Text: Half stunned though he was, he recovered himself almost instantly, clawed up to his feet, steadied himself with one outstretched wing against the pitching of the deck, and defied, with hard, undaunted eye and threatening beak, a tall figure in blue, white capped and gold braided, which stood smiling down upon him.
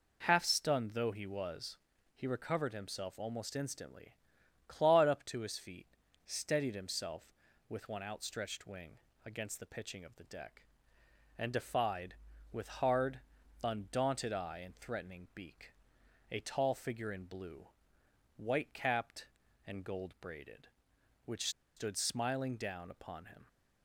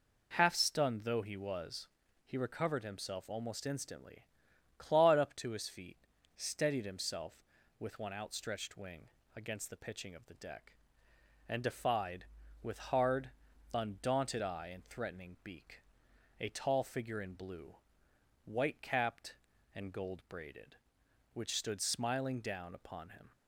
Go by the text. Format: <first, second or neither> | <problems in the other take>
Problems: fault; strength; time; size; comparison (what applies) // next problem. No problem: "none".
second | pauses between "wing" and "against"; slight; at 8.9 s; 0.26 s long; slight in the second // pauses between "which" and "stood"; slight; at 21.4 s; 0.27 s long